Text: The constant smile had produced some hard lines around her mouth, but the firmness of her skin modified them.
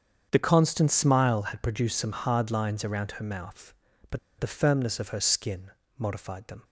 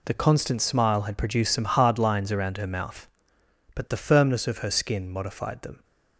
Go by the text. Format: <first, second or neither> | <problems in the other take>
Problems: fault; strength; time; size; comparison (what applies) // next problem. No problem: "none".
second | starts louder than the rest; strong; until 1.3 s; 7.5 dB // pauses between "but" and "the"; slight; at 4.1 s; 0.20 s long // pauses between "skin" and "modified"; slight; at 5.7 s; 0.26 s long